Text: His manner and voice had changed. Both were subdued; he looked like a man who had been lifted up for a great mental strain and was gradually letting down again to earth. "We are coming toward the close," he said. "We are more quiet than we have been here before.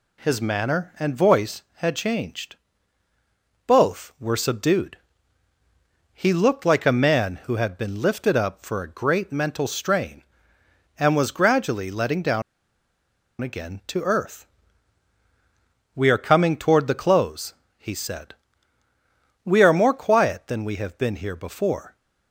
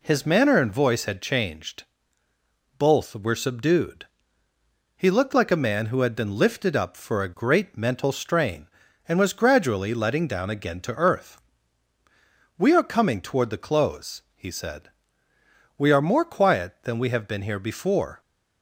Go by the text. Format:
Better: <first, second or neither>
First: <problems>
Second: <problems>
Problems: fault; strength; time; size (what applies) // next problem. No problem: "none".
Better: second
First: pauses between "down" and "again"; at 12.4 s; 0.99 s long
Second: none